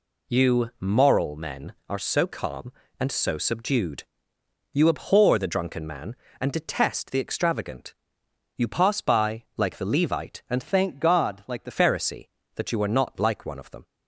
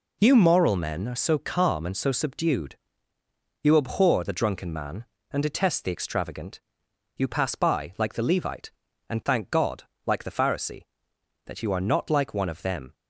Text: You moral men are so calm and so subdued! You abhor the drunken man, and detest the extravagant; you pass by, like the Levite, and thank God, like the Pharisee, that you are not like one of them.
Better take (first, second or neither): second